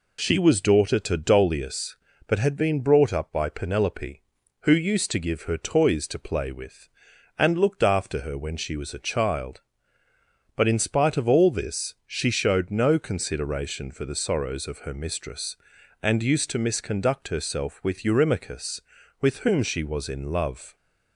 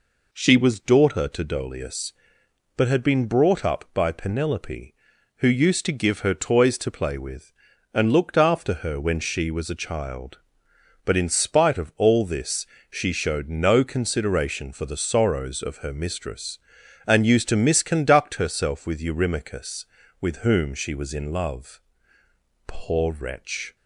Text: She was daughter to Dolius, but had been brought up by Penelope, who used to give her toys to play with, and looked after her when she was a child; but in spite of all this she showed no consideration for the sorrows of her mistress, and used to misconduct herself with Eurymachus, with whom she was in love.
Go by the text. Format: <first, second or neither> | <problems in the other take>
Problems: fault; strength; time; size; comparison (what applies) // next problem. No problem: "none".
first | pauses between "this" and "she"; slight; at 12.6 s; 0.24 s long // goes on to say "Poor wretch"; noticeable; from 22.6 s on; 1.0 s long